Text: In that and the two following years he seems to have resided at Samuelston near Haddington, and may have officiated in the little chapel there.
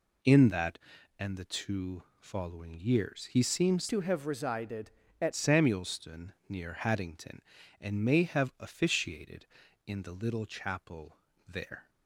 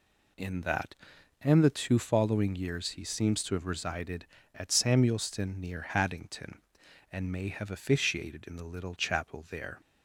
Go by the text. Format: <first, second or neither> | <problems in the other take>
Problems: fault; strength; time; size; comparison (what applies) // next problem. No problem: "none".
second | pauses between "two" and "following"; slight; at 2.0 s; 0.16 s long // changes voice from "to" to "at"; from 3.8 to 5.3 s; 1.5 s long // pauses between "chapel" and "there"; slight; at 11.1 s; 0.32 s long